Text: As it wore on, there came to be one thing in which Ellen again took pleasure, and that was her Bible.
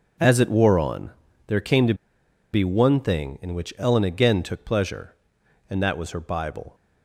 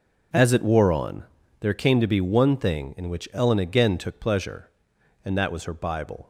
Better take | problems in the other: second | pauses between "to" and "be"; noticeable; at 1.9 s; 0.59 s long

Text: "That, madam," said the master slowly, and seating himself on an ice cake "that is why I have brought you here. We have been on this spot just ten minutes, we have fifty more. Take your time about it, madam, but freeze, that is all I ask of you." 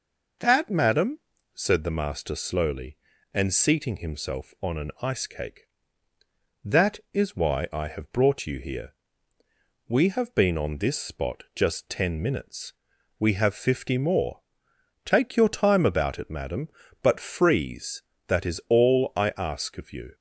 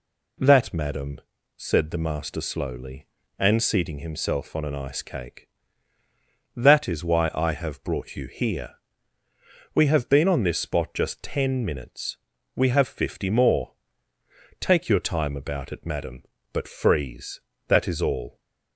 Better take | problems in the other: first | stops before "I ask of you"; at 18.3 s

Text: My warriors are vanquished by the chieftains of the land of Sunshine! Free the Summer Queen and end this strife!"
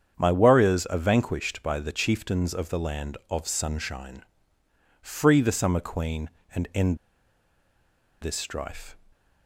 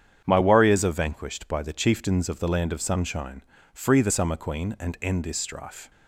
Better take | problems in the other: second | starts louder than the rest; strong; until 1.1 s; 8 dB; strong in the second // pauses between "end" and "this"; strong; at 6.9 s; 1.2 s long

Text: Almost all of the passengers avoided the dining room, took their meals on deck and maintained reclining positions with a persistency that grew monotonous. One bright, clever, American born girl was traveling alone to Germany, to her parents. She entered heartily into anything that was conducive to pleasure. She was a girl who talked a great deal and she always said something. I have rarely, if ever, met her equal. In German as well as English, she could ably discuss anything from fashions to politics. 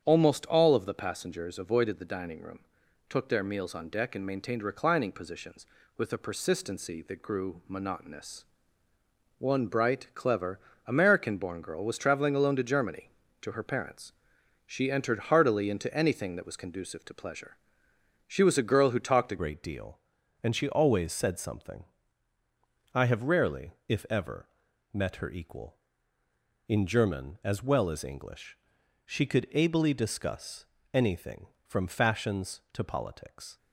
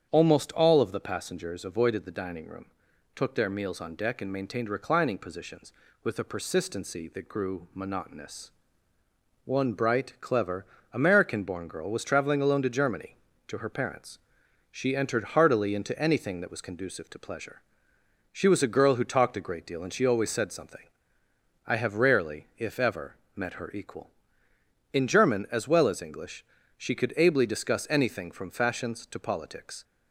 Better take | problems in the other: second | starts louder than the rest; strong; until 1.0 s; 8.5 dB; strong in the second // changes voice at "great"; from 19.3 s on; 14.2 s long // pauses between "discuss" and "anything"; slight; at 30.6 s; 0.26 s long

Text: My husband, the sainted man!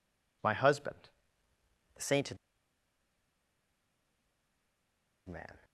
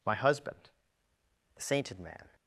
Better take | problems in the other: second | pauses between "sainted" and "man"; strong; at 2.3 s; 2.9 s long

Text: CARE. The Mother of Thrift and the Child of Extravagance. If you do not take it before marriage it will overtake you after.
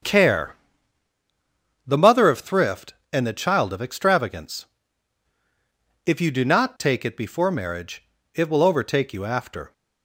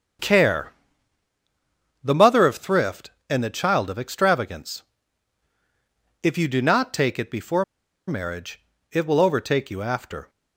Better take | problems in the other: first | starts louder than the rest; strong; until 2.5 s; 7 dB; strong in the first // pauses between "before" and "marriage"; at 7.6 s; 0.43 s long // pauses between "marriage" and "it"; slight; at 8.6 s; 0.28 s long; slight in the first

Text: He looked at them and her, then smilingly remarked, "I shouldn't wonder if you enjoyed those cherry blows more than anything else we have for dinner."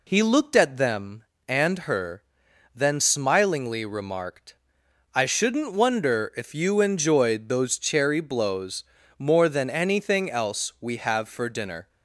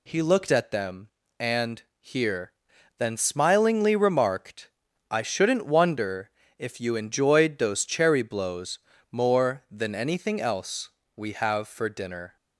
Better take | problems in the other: first | says "here" for "her"; at 1.9 s // pauses between "wonder" and "if"; slight; at 6.2 s; 0.30 s long // pauses between "blows" and "more"; slight; at 8.7 s; 0.32 s long; slight in the first // pauses between "else" and "we"; slight; at 10.8 s; 0.26 s long

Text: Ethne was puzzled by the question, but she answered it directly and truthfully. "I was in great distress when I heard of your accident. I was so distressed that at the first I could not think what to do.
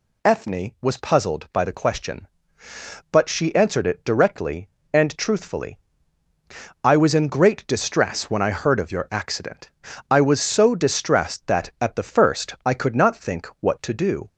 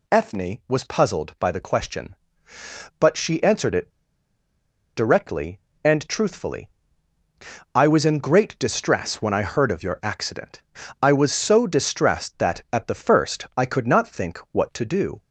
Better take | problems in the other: first | pauses between "it" and "directly"; at 3.9 s; 1.0 s long

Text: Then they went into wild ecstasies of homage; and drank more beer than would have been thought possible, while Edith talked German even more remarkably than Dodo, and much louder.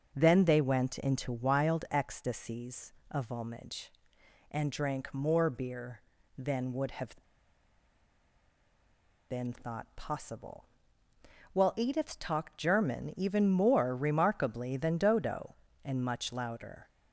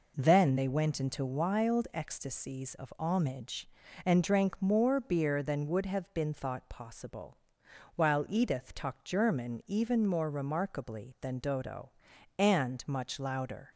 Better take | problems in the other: second | starts louder than the rest; until 1.1 s; 6.5 dB // pauses between "have" and "been"; strong; at 7.1 s; 2.1 s long

